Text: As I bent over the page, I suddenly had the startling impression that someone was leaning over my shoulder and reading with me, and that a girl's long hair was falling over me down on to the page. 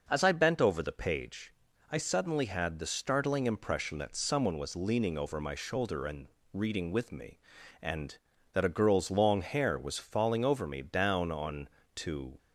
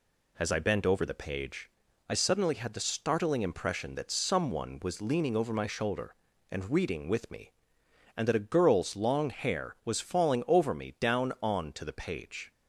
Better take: second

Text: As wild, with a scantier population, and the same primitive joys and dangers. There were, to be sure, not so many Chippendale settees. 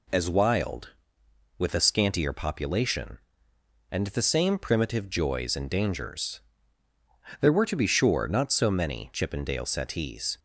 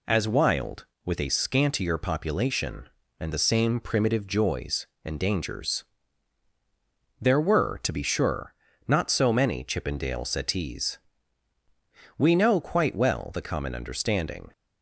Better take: first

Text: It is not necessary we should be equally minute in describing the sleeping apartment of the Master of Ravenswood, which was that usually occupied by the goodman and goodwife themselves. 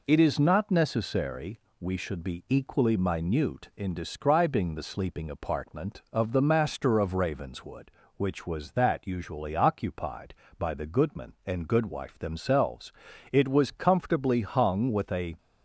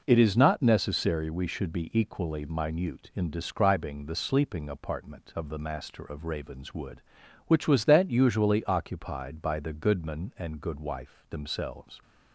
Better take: second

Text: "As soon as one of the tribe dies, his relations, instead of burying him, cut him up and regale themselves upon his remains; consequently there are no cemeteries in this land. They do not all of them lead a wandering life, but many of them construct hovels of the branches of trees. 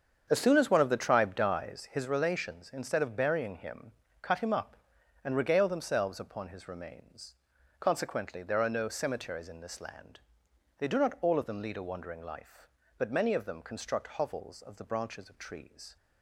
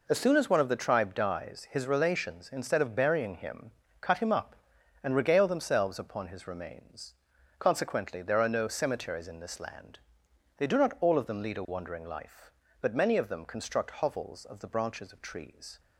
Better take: second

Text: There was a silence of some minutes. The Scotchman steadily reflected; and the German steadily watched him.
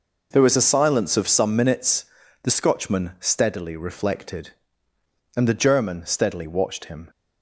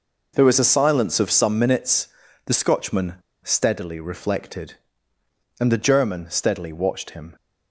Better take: first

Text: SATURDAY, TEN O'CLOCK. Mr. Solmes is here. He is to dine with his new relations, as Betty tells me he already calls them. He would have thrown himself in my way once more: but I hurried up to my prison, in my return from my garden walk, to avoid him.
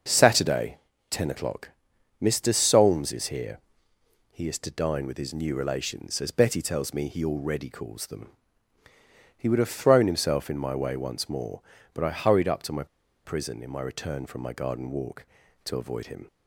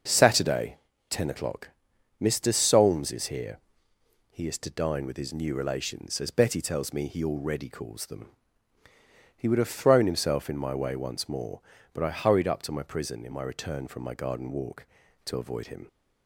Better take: second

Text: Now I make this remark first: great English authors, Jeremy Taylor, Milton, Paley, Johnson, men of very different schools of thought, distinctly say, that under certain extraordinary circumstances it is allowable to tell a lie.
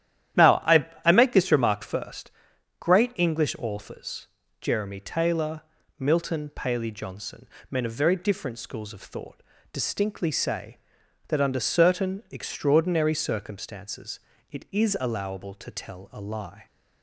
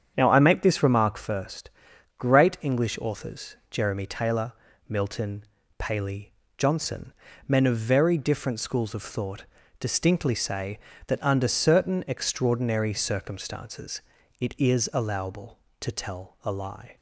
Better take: second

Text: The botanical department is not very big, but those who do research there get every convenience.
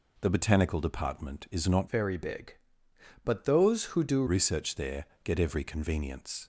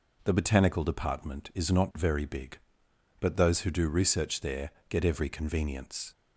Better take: second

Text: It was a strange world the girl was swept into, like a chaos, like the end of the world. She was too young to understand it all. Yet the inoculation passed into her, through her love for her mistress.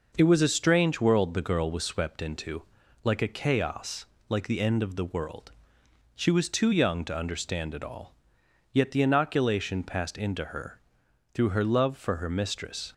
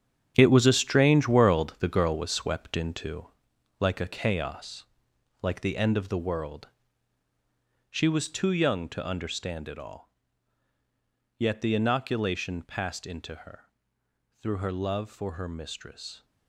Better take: first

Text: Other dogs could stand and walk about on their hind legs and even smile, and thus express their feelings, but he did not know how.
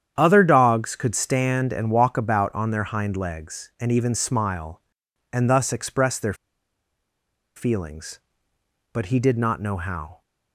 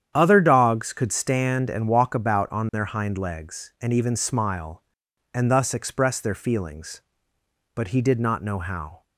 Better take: second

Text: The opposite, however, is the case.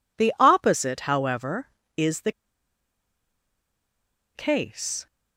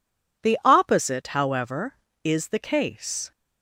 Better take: second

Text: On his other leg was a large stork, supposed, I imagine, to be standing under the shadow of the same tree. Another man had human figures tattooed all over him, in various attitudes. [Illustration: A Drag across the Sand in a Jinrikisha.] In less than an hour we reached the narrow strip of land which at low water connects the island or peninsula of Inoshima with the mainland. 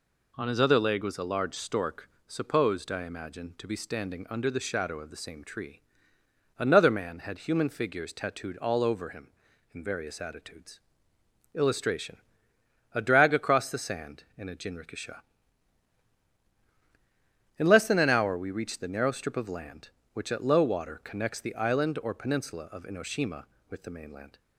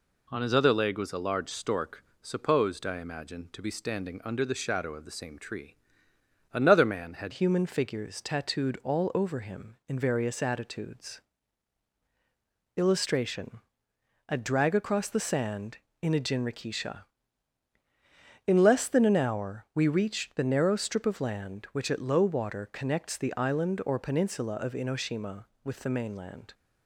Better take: first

